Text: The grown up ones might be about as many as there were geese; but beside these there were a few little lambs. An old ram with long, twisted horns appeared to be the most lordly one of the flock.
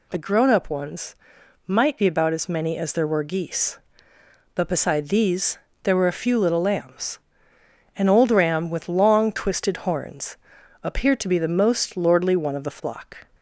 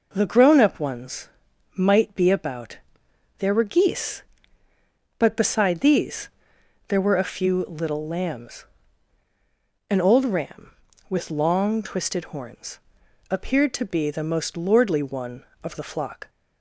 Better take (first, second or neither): first